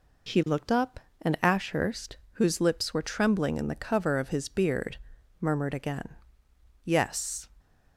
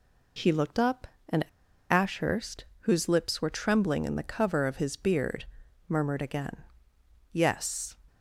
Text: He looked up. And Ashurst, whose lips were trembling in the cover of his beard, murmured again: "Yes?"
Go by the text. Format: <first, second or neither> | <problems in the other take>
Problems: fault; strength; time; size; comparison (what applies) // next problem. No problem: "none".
first | pauses between "And" and "Ashurst"; noticeable; at 1.4 s; 0.47 s long